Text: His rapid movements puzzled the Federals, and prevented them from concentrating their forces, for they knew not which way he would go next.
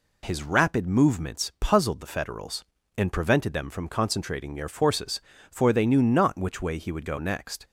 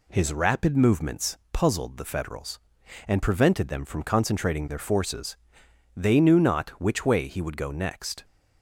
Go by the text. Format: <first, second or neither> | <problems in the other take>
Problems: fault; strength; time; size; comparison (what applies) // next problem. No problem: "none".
first | skips "for"; at 5.6 s